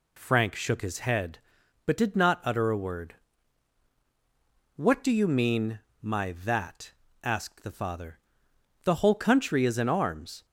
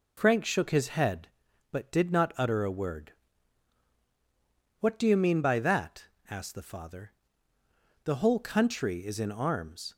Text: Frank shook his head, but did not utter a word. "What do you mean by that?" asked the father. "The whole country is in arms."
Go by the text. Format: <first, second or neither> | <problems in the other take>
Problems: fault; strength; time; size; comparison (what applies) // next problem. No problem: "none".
second | says "my" for "by"; at 6.0 s